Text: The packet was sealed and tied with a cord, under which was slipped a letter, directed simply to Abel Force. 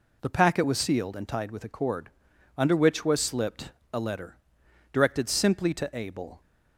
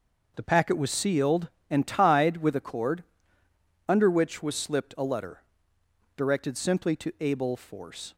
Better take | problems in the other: second | pauses between "slipped" and "a"; slight; at 3.7 s; 0.22 s long // stops before "Force"; at 6.4 s

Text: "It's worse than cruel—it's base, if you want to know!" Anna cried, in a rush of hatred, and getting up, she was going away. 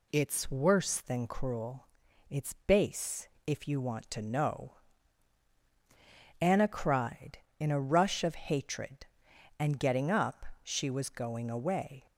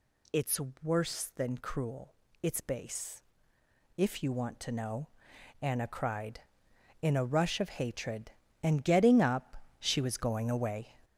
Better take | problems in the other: first | gets louder; throughout; 4 dB // pauses between "It's" and "worse"; slight; at 0.5 s; 0.24 s long

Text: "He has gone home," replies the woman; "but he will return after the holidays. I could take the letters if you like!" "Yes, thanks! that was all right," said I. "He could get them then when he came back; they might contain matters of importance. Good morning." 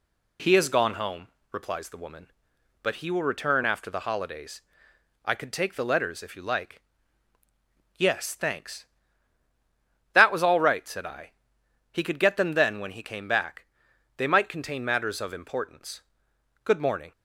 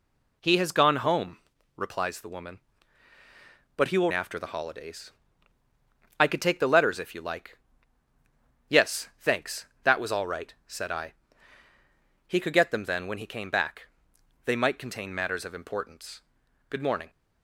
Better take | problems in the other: first | skips "return"; at 4.1 s

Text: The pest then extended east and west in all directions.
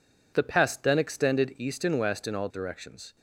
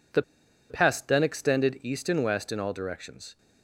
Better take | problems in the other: first | pauses between "The" and "pest"; noticeable; at 0.2 s; 0.47 s long

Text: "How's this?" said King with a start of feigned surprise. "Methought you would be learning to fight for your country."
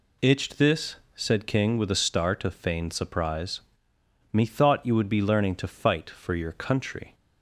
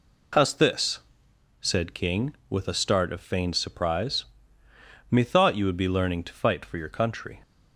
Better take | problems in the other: second | says "Itched" for "How's"; at 0.2 s

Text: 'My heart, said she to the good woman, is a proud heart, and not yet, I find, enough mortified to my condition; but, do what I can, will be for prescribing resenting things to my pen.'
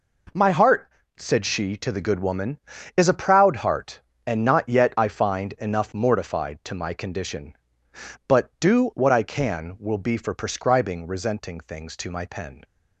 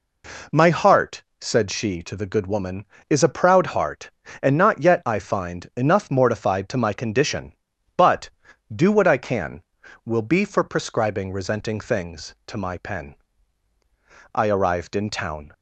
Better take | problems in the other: first | goes on to say "I arrived in town"; noticeable; from 14.3 s on; 1.2 s long

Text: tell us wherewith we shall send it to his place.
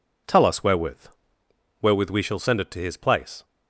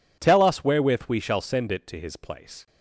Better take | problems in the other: second | says "wherewith" twice; at 1.8 s

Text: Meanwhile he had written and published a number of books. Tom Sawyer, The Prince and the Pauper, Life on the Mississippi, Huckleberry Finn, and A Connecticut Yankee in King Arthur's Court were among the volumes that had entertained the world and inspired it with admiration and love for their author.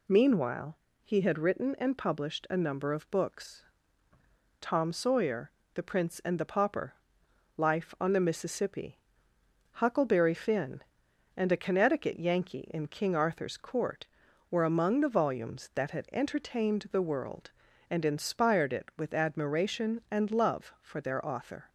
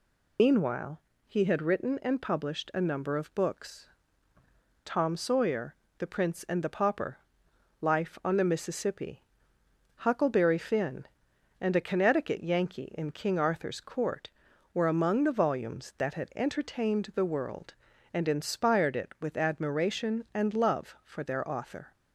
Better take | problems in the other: first | loses the start of "Meanwhile"; at 0.3 s; 75 ms // pauses between "Meanwhile" and "he"; slight; at 1.0 s; 0.26 s long; slight in the first

